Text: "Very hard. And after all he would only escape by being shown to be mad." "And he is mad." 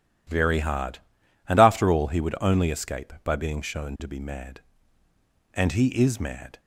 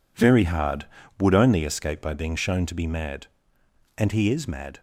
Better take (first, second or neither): first